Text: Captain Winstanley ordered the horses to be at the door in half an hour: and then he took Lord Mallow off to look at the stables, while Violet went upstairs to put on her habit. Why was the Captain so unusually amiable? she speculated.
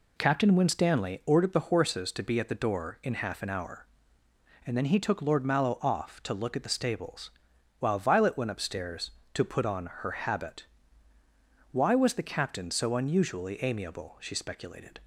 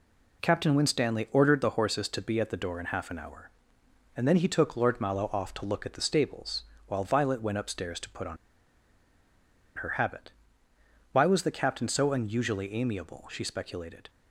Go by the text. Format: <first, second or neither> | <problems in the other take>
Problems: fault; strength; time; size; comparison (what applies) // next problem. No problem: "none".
first | pauses between "on" and "her"; strong; at 8.3 s; 1.4 s long